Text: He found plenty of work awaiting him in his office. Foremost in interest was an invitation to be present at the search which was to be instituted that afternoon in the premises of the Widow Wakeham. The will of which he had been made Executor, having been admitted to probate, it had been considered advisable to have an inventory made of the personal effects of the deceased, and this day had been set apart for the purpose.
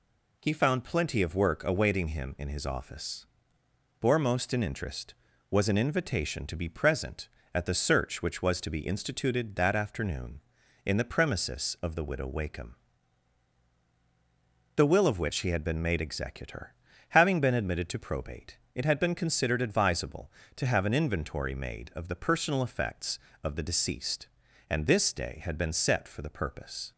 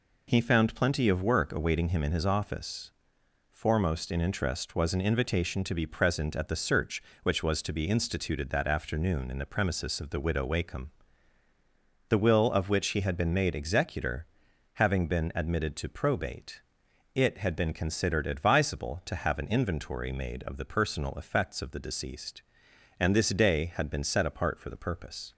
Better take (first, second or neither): second